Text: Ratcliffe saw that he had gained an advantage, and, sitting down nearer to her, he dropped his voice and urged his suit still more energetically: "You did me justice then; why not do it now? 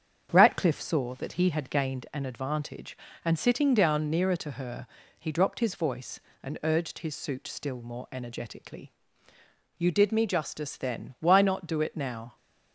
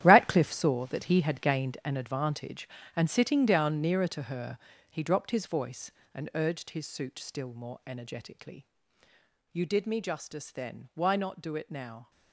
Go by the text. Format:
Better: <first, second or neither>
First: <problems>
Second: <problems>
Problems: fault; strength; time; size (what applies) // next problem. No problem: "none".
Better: first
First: starts louder than the rest; strong; until 1.3 s; 7.5 dB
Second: gets quieter; strong; throughout; 13 dB // starts louder than the rest; strong; until 1.0 s; 11.5 dB